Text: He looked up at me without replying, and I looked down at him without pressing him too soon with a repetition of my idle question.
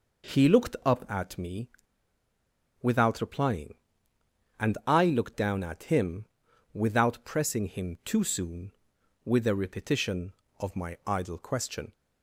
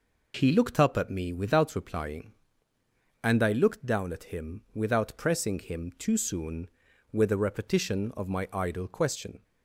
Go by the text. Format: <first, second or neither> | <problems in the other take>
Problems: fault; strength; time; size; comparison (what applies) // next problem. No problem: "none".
second | pauses between "me" and "without"; at 1.6 s; 1.1 s long // pauses between "him" and "without"; noticeable; at 6.2 s; 0.48 s long